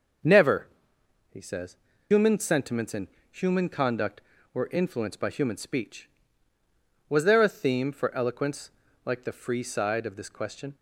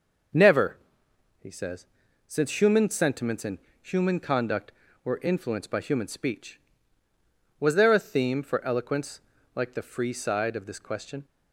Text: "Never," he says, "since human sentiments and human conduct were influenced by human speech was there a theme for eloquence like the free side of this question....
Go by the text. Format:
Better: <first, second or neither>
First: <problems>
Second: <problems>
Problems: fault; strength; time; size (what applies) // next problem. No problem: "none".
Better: second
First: starts louder than the rest; until 2.2 s; 6.5 dB // skips "since"; at 1.9 s // pauses between "and" and "human"; slight; at 3.0 s; 0.24 s long // pauses between "eloquence" and "like"; slight; at 8.6 s; 0.36 s long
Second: pauses between "and" and "human"; slight; at 3.5 s; 0.24 s long // pauses between "eloquence" and "like"; slight; at 9.1 s; 0.36 s long